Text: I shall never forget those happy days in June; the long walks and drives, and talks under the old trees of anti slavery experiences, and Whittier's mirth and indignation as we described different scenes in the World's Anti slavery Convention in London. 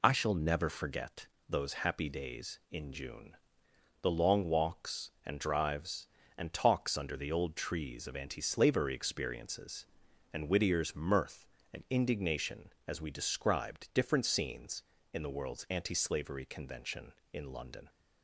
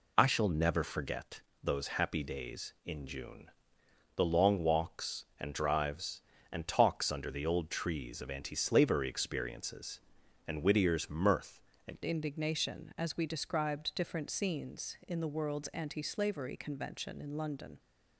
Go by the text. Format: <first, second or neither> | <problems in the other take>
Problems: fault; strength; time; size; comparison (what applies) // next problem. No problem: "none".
first | pauses between "forget" and "those"; slight; at 1.4 s; 0.20 s long; slight in the first // changes voice at "indignation"; from 12.0 s on; 5.7 s long